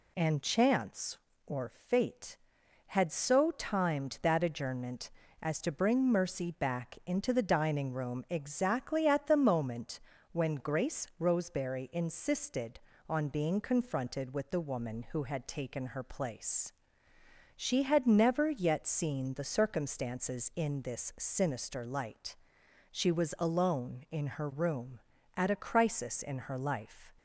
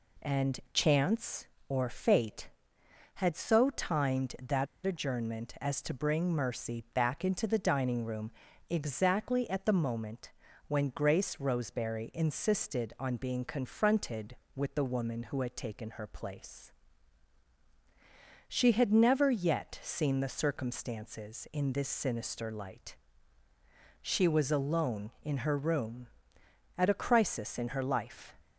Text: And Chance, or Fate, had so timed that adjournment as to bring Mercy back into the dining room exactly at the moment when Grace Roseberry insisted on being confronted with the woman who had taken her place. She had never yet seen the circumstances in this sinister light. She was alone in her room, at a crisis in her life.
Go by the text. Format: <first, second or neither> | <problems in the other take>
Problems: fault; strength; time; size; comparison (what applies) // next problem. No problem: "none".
first | pauses between "that" and "adjournment"; slight; at 4.6 s; 0.19 s long // pauses between "room" and "exactly"; at 8.2 s; 0.40 s long // pauses between "moment" and "when"; at 10.2 s; 0.38 s long; slight in the first